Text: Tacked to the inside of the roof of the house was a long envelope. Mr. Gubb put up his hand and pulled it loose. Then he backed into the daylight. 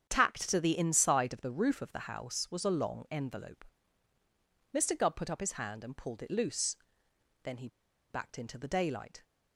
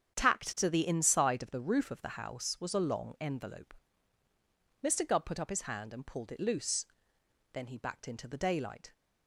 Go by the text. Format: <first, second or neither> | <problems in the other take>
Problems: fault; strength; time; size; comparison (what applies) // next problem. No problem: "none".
second | starts louder than the rest; strong; until 1.1 s; 8 dB; strong in the second // pauses between "he" and "backed"; at 7.6 s; 0.42 s long